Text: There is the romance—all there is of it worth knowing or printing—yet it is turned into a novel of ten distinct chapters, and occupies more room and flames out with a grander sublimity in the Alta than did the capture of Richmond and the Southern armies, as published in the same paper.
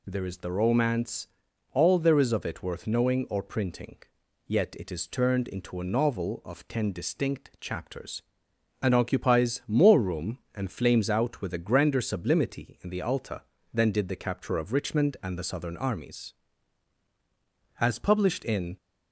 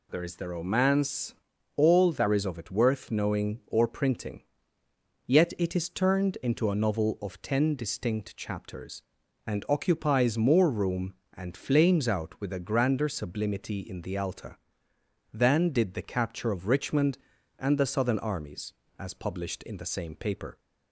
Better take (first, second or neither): second